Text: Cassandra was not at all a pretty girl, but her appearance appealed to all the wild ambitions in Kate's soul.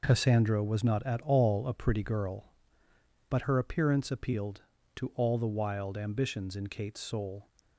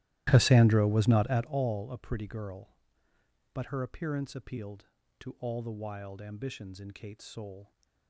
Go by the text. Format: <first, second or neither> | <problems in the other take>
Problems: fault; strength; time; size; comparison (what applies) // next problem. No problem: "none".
first | starts louder than the rest; strong; until 1.6 s; 14.5 dB